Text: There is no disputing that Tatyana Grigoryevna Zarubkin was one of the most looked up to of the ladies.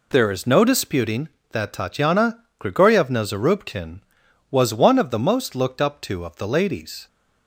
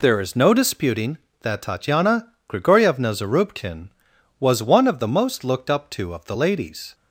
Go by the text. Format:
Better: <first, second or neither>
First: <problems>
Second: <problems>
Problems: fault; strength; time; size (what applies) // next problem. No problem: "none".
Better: neither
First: pauses between "Tatyana" and "Grigoryevna"; slight; at 2.3 s; 0.20 s long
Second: pauses between "Tatyana" and "Grigoryevna"; slight; at 2.2 s; 0.20 s long